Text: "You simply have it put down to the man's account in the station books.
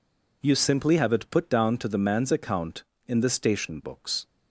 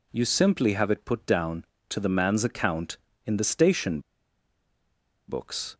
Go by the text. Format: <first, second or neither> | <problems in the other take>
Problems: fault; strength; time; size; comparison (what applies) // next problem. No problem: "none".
first | pauses between "station" and "books"; strong; at 4.0 s; 1.2 s long